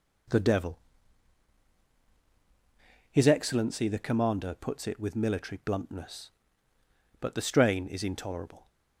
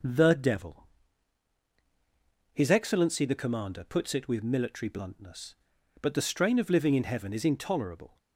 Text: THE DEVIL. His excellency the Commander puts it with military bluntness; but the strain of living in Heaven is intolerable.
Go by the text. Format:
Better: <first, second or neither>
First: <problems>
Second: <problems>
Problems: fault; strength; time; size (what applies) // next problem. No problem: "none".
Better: second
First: skips "of living in Heaven"; at 7.8 s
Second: none